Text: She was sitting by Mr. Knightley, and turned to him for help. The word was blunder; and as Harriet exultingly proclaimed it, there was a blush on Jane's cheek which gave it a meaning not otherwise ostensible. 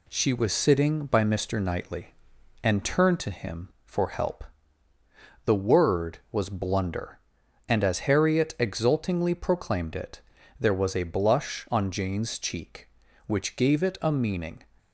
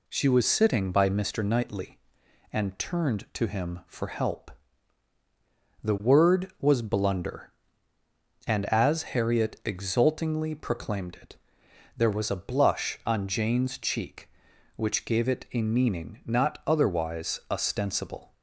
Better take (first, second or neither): second